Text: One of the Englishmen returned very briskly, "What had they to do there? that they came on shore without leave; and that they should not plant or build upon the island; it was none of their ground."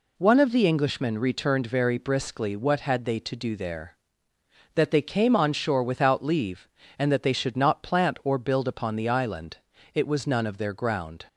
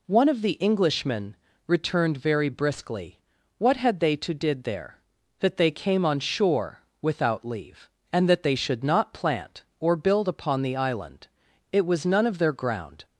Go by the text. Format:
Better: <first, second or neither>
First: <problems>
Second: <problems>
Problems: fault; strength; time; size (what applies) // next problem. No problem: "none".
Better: first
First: none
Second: pauses between "Englishmen" and "returned"; slight; at 1.3 s; 0.28 s long // says "did" for "do"; at 4.3 s // pauses between "shore" and "without"; slight; at 6.8 s; 0.20 s long